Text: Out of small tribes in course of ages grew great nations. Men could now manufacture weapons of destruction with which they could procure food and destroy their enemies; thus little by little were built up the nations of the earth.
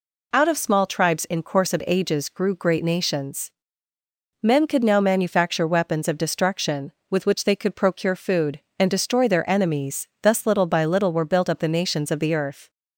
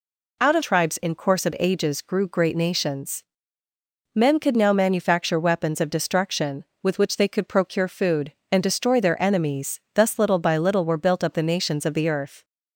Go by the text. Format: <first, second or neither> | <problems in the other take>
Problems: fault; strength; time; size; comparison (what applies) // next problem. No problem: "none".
first | skips "small"; at 0.6 s